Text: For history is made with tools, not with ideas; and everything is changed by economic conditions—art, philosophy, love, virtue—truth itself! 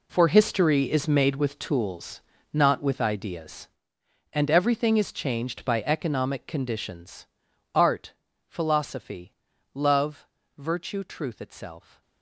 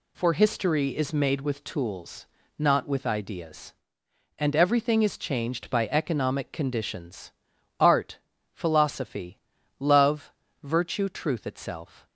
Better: second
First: gets quieter; strong; throughout; 14 dB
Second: none

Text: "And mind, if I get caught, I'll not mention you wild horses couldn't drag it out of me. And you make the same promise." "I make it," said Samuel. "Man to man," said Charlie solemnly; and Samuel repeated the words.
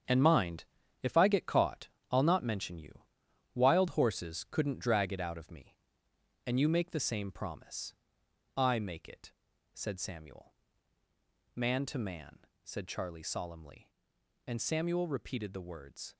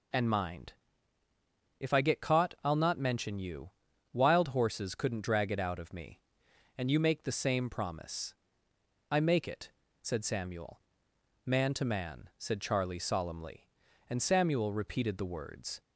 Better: second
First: gets quieter; strong; throughout; 9.5 dB // pauses between "you" and "wild"; noticeable; at 3.0 s; 0.54 s long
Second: pauses between "you" and "wild"; at 3.7 s; 0.42 s long

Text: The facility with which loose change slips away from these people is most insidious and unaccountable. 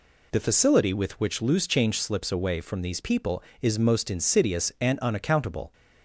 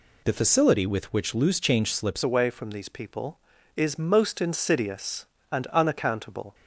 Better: first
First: none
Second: changes voice at "away"; from 2.2 s on; 4.3 s long

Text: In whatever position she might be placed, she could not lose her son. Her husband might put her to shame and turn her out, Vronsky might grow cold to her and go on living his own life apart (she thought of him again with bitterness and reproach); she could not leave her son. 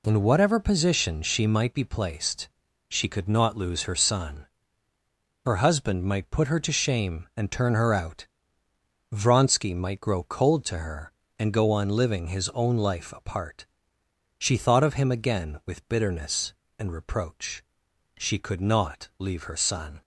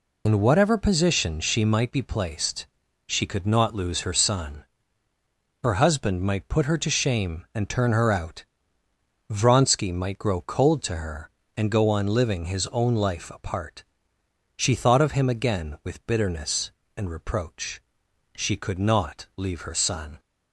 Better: first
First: none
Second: loses the start of "In"; at 0.2 s; 30 ms

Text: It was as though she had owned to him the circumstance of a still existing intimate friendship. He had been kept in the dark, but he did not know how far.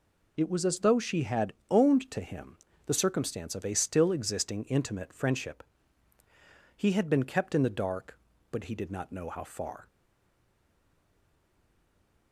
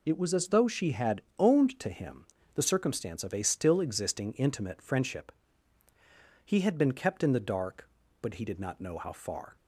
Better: second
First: pauses between "had" and "owned"; slight; at 1.5 s; 0.16 s long // pauses between "him" and "the"; slight; at 2.5 s; 0.30 s long // stays silent after the last word; from 9.8 s on; 2.5 s long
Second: pauses between "had" and "owned"; slight; at 1.2 s; 0.16 s long // pauses between "him" and "the"; slight; at 2.2 s; 0.30 s long

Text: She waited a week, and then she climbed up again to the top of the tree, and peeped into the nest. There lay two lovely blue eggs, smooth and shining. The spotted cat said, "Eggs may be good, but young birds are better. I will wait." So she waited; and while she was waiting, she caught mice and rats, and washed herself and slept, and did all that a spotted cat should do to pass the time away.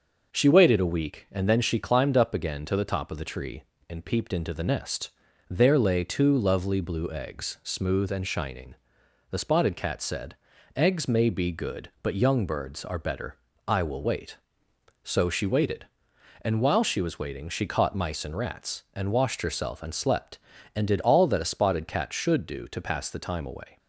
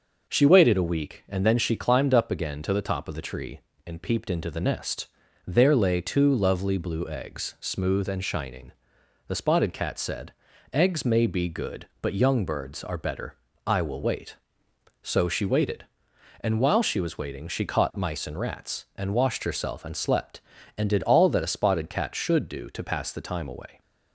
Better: neither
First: none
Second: none

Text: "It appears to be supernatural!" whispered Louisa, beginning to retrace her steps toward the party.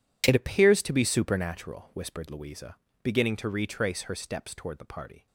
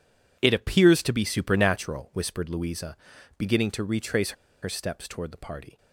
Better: first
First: none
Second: pauses between "retrace" and "her"; slight; at 4.3 s; 0.33 s long

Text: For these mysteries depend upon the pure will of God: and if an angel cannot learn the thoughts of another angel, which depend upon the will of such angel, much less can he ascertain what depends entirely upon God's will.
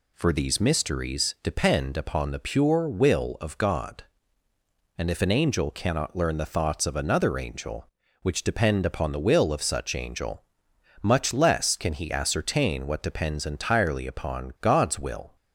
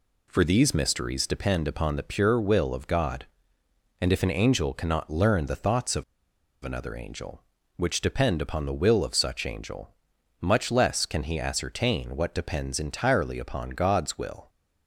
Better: first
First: none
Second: pauses between "of" and "another"; noticeable; at 6.0 s; 0.59 s long

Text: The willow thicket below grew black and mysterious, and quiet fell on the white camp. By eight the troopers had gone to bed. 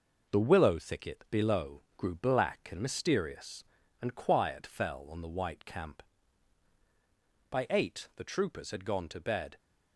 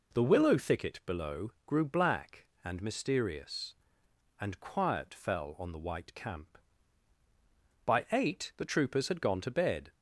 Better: second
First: gets quieter; noticeable; throughout; 5 dB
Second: none

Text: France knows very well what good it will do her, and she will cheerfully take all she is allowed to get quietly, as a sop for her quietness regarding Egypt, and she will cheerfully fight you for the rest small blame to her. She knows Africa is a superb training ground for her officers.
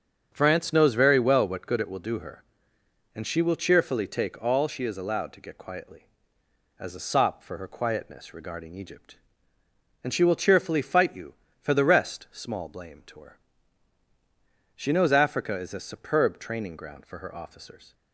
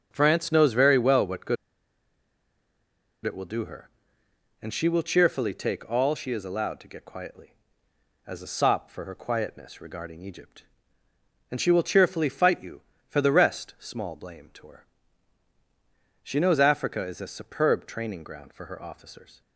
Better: first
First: starts louder than the rest; until 1.3 s; 7 dB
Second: starts louder than the rest; until 1.1 s; 7 dB // pauses between "good" and "it"; strong; at 1.5 s; 1.6 s long

